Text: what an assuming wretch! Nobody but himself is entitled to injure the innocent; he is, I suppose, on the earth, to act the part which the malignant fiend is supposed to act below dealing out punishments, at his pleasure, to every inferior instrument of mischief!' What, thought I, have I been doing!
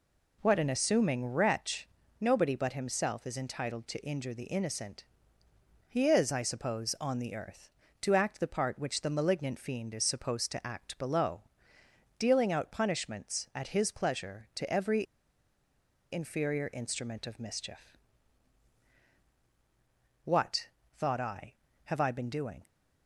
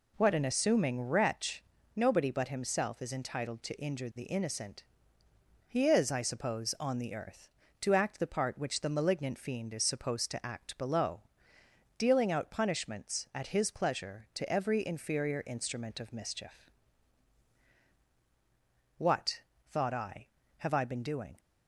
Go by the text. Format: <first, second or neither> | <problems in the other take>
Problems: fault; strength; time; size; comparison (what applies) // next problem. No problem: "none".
second | pauses between "below" and "dealing"; noticeable; at 11.4 s; 0.78 s long; noticeable in the second // pauses between "every" and "inferior"; at 15.0 s; 1.0 s long